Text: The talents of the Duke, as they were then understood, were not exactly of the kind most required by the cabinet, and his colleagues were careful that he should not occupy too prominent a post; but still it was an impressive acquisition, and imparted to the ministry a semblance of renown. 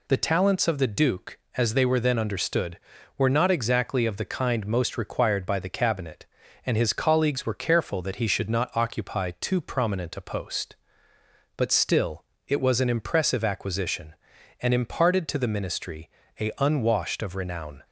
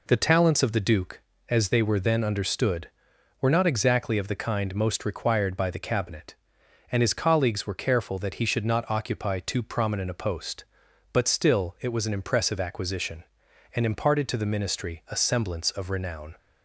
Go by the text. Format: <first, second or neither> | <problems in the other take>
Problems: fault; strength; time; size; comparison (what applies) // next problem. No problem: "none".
second | pauses between "still" and "it"; slight; at 12.2 s; 0.24 s long // pauses between "ministry" and "a"; slight; at 16.0 s; 0.32 s long // says "unwashed" for "semblance"; at 16.5 s